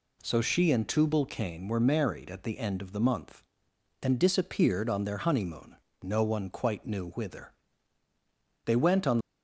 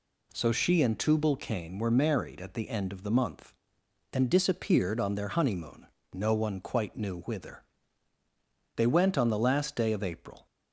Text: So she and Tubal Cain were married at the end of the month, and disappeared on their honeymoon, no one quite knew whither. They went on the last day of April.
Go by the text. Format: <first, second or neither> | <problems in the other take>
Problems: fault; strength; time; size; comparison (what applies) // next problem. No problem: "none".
second | stops before "the last day of April"; at 9.2 s